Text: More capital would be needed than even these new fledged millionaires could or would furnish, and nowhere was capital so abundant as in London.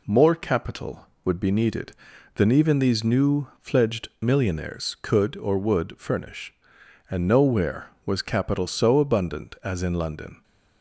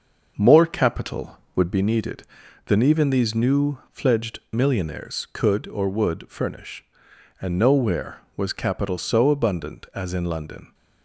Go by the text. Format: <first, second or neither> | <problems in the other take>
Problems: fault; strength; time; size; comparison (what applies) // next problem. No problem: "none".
first | starts louder than the rest; until 1.9 s; 6 dB